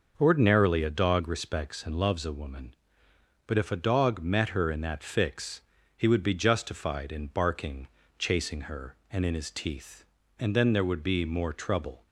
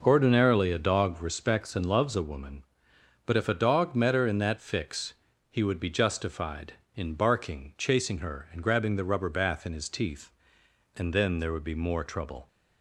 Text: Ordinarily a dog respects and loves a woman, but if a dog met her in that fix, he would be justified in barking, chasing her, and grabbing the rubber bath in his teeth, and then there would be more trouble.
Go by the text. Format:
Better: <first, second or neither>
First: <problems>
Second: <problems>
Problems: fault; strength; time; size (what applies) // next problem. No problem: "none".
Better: second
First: skips "grabbing the rubber bath"; at 9.2 s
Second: none